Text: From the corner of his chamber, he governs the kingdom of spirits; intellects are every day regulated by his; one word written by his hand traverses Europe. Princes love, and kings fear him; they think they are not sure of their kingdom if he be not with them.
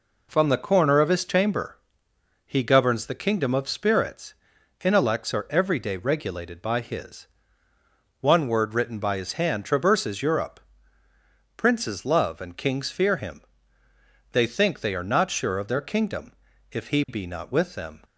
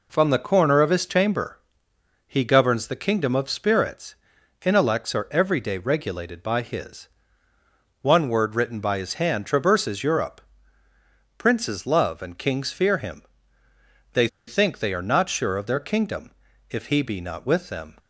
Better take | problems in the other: first | pauses between "they" and "think"; slight; at 14.2 s; 0.20 s long // pauses between "kingdom" and "if"; at 16.3 s; 0.38 s long; also in the first

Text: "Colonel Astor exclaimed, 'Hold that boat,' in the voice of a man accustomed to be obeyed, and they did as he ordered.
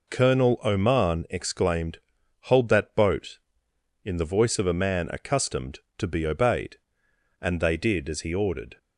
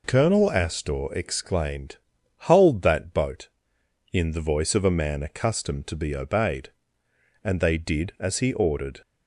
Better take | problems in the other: second | says "Oman" for "Astor"; at 0.6 s

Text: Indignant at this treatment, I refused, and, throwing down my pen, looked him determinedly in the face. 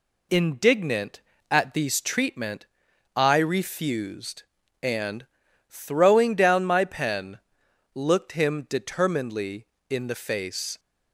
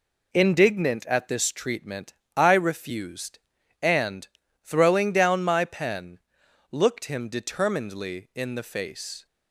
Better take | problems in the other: second | says "these" for "this"; at 1.7 s

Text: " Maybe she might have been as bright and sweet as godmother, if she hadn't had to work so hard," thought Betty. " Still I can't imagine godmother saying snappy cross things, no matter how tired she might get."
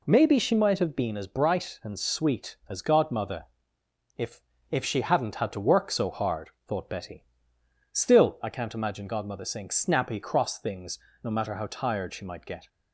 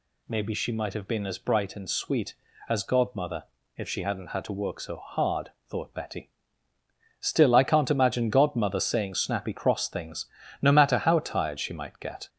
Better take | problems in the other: second | says "if" twice; at 4.6 s

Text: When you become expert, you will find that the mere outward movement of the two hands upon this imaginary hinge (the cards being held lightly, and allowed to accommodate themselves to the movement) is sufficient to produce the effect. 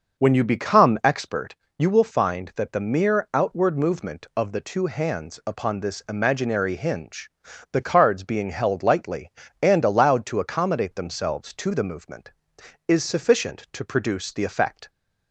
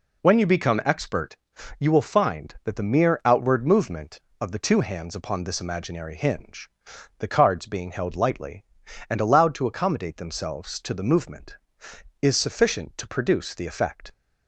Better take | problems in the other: second | starts louder than the rest; noticeable; until 1.4 s; 6 dB

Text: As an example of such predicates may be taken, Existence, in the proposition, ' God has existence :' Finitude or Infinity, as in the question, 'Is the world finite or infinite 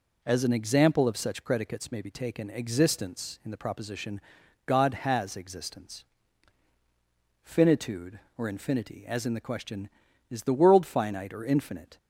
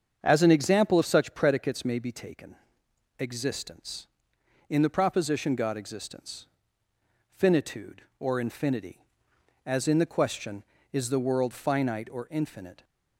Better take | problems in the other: first | starts louder than the rest; strong; until 1.2 s; 7.5 dB // skips "has"; at 5.7 s

